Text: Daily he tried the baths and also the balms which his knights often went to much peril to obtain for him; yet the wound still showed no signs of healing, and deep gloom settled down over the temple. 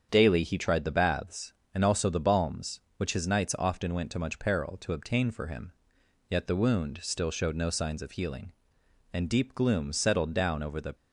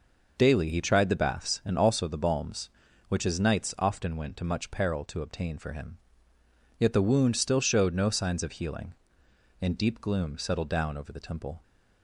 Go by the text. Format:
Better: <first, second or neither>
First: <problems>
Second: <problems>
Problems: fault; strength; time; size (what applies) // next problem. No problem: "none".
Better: second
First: starts louder than the rest; strong; until 1.1 s; 7.5 dB // stops before "temple"; at 10.9 s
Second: none